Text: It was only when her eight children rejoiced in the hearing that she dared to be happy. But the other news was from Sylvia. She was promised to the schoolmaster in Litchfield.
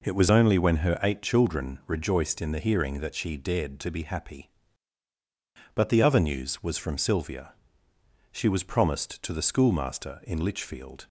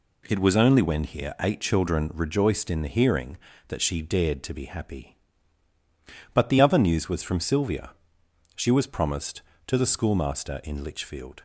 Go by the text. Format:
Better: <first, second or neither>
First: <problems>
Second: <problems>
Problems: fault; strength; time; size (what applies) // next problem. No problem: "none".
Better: first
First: none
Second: says "here" for "her"; at 1.0 s